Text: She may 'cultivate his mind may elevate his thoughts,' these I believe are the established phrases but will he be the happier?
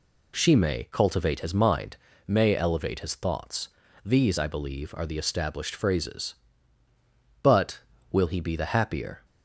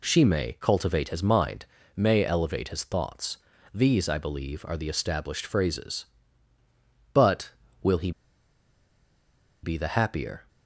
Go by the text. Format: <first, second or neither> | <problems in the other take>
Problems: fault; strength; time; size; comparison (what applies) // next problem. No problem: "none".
first | pauses between "mind" and "may"; slight; at 1.6 s; 0.30 s long; slight in the first // pauses between "he" and "be"; strong; at 8.1 s; 1.5 s long